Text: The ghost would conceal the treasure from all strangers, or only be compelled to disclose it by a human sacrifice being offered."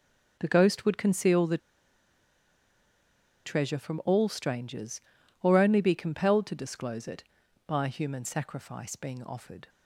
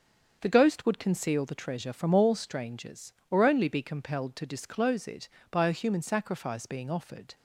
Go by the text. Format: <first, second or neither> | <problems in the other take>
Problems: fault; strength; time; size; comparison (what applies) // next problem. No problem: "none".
second | starts louder than the rest; until 1.4 s; 6.5 dB; also in the second // pauses between "the" and "treasure"; strong; at 1.5 s; 1.8 s long